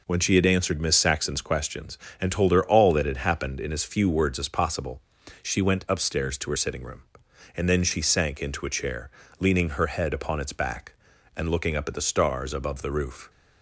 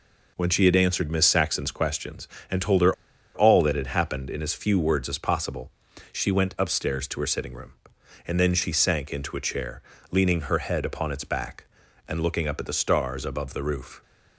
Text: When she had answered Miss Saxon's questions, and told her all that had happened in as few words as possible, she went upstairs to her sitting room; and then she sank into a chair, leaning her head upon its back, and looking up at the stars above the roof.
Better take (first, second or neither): first